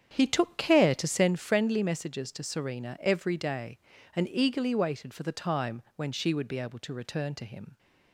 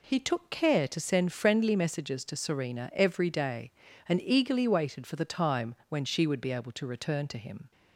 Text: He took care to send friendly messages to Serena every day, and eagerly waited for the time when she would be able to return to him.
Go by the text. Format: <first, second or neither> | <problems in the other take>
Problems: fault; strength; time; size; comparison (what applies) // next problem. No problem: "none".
second | starts louder than the rest; strong; until 1.4 s; 8.5 dB